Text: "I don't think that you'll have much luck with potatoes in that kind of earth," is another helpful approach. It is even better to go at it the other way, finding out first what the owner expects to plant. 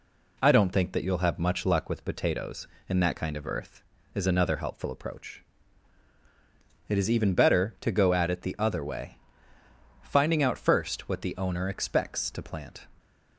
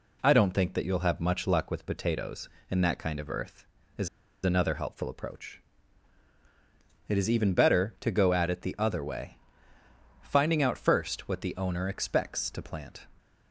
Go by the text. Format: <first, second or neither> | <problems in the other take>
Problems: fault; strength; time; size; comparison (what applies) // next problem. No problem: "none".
first | pauses between "is" and "another"; slight; at 4.0 s; 0.35 s long